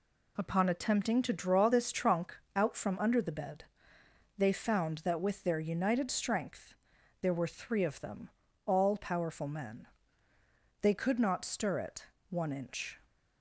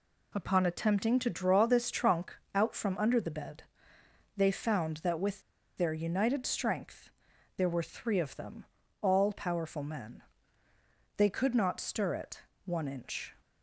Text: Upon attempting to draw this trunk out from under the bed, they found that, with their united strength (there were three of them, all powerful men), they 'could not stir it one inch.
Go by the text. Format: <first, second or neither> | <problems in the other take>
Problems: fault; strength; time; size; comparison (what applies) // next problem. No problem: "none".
first | pauses between "trunk" and "out"; slight; at 2.3 s; 0.22 s long; slight in the first // pauses between "with" and "their"; slight; at 5.4 s; 0.35 s long // pauses between "it" and "one"; slight; at 12.4 s; 0.24 s long; slight in the first